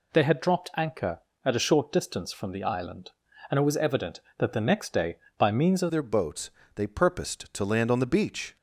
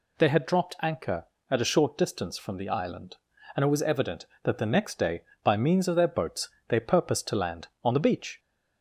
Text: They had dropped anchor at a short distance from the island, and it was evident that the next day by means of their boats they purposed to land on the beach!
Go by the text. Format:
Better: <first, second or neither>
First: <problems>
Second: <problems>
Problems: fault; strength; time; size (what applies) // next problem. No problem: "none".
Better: second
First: changes voice at "their"; from 5.9 s on; 2.6 s long // pauses between "boats" and "they"; slight; at 6.5 s; 0.24 s long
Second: pauses between "boats" and "they"; slight; at 6.4 s; 0.22 s long